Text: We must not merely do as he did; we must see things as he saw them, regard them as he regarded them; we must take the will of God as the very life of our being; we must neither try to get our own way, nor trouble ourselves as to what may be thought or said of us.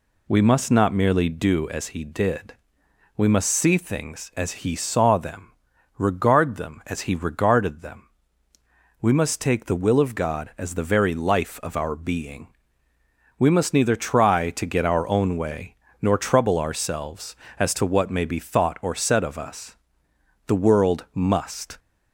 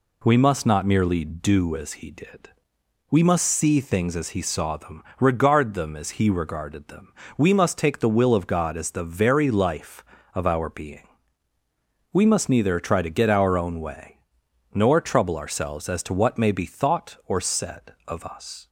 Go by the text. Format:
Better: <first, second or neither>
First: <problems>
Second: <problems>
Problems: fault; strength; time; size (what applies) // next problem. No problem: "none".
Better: second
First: goes on to say "The world must"; from 20.4 s on; 1.3 s long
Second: none